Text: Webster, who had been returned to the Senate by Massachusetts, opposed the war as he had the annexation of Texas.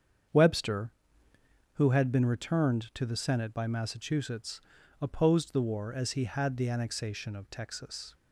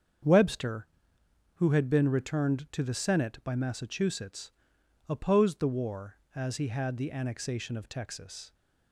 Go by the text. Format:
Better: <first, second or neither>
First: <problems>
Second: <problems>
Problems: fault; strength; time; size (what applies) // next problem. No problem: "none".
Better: neither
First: starts louder than the rest; strong; until 2.1 s; 7.5 dB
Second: starts louder than the rest; strong; until 1.9 s; 7 dB